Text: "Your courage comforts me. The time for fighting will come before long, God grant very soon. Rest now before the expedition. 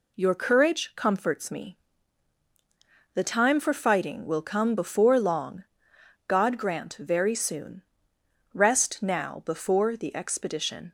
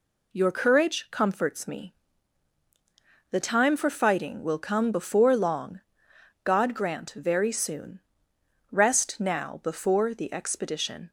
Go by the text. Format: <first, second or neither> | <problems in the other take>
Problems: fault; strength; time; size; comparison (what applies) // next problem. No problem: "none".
neither | none